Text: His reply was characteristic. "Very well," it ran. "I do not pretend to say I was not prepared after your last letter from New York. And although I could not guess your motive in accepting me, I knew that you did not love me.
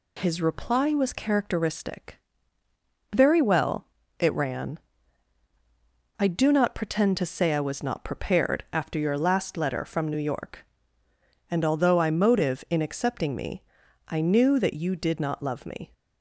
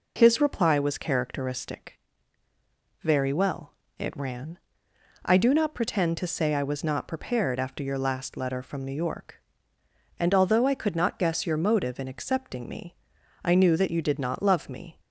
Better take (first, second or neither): second